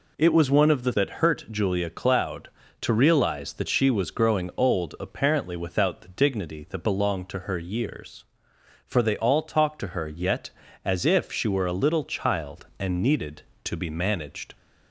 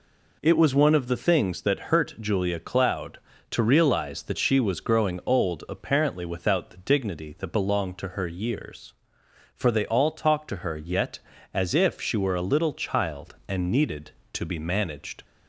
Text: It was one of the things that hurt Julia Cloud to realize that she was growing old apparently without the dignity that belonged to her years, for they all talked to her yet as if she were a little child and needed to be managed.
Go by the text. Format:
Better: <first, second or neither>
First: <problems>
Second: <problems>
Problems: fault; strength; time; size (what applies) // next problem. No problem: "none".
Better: second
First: skips "things"; at 0.9 s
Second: none